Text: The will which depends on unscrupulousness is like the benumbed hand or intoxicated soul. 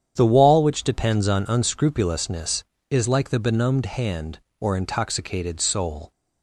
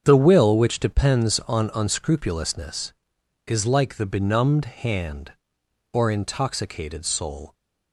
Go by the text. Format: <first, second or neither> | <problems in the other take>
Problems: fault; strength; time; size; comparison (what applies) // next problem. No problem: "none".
second | starts louder than the rest; strong; until 1.1 s; 9 dB; strong in the second // says "wall" for "will"; at 0.3 s